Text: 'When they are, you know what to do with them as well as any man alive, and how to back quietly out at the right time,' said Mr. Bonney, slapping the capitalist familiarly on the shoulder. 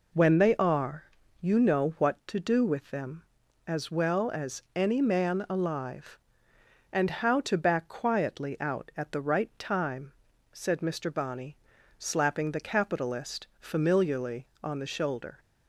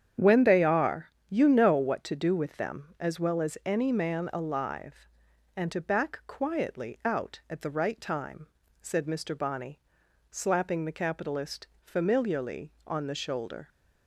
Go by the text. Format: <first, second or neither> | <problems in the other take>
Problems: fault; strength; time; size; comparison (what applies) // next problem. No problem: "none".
first | starts louder than the rest; strong; until 1.3 s; 8.5 dB // skips "how"; at 5.7 s // pauses between "capitalist" and "familiarly"; slight; at 11.6 s; 0.16 s long